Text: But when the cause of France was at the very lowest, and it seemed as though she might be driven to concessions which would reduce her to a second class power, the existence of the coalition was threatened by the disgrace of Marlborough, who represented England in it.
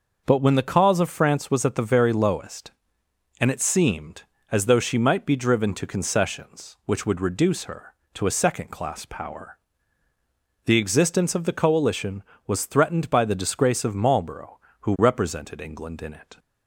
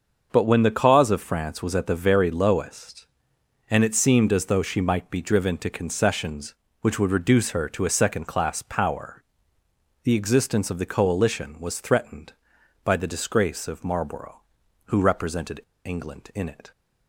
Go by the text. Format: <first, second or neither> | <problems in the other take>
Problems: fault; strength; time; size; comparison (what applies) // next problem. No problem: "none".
first | starts louder than the rest; until 1.3 s; 6.5 dB // pauses between "represented" and "England"; slight; at 15.5 s; 0.25 s long